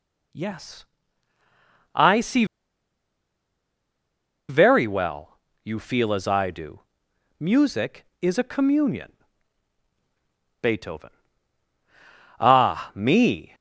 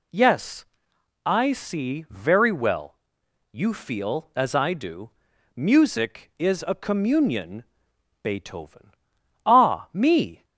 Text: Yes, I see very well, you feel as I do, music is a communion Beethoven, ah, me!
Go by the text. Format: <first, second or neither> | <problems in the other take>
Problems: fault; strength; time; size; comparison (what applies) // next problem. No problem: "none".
second | pauses between "see" and "very"; strong; at 2.4 s; 2.0 s long // pauses between "communion" and "Beethoven"; strong; at 9.1 s; 1.4 s long; noticeable in the second